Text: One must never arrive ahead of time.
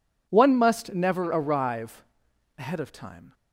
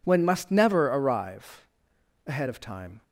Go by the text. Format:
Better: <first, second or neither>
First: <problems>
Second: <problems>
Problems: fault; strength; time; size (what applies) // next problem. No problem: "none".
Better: first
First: pauses between "arrive" and "ahead"; noticeable; at 2.0 s; 0.54 s long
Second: says "When" for "One"; at 0.0 s // pauses between "arrive" and "ahead"; noticeable; at 1.6 s; 0.62 s long